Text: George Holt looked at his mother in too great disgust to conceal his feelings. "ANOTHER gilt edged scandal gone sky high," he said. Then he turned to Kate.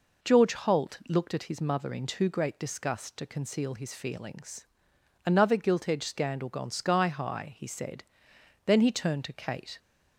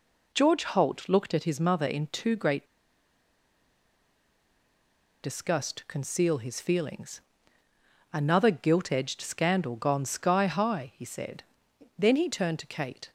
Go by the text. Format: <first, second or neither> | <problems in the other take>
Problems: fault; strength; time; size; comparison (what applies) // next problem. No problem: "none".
first | pauses between "great" and "disgust"; strong; at 2.6 s; 2.5 s long